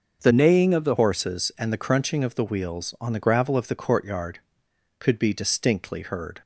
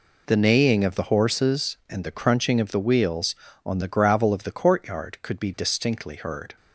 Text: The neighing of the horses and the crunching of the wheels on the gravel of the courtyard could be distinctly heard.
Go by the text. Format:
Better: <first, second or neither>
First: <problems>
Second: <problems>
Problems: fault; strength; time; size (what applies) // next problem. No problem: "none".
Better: second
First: starts louder than the rest; noticeable; until 1.2 s; 6 dB // changes voice from "neighing" to "the"; from 0.3 to 0.9 s; 0.6 s long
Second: none